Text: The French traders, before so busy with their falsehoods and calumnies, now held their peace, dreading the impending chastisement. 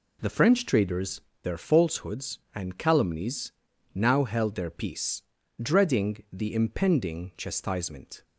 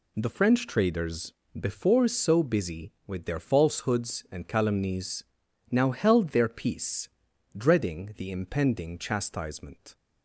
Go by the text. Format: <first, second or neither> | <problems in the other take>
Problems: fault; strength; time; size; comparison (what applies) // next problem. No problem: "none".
second | skips "before so busy with"; at 1.3 s